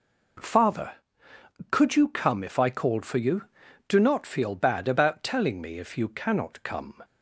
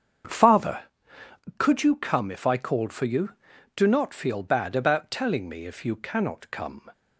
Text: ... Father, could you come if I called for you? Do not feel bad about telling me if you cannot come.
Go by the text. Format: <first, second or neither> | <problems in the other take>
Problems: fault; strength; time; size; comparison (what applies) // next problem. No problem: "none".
first | starts louder than the rest; strong; until 1.6 s; 7.5 dB